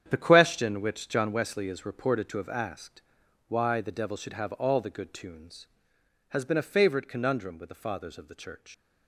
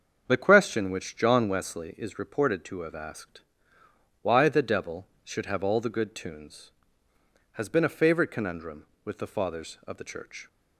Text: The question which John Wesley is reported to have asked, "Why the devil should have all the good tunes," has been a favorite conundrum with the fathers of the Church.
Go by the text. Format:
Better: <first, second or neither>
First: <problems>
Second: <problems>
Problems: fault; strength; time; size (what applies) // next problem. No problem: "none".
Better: second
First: starts louder than the rest; strong; until 1.0 s; 9 dB // leaves "Church" unfinished; at 8.7 s; 115 ms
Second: starts louder than the rest; until 1.2 s; 7 dB